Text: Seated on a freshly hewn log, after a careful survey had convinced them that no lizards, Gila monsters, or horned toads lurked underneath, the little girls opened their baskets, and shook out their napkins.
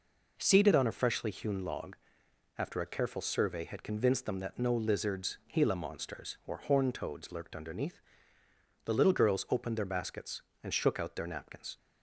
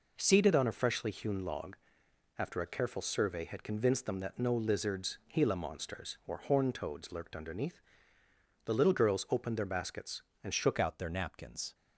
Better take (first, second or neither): first